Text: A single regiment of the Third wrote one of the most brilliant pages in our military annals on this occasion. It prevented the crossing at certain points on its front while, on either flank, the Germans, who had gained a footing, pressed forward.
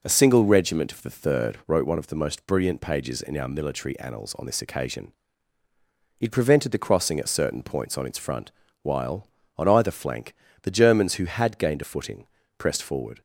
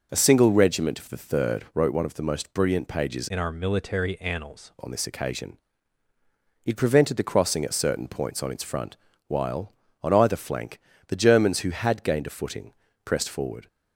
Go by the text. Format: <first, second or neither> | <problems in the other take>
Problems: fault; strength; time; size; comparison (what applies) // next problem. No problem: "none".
first | changes voice from "in" to "annals"; from 3.2 to 4.7 s; 1.5 s long // pauses between "front" and "while"; slight; at 8.9 s; 0.32 s long; slight in the first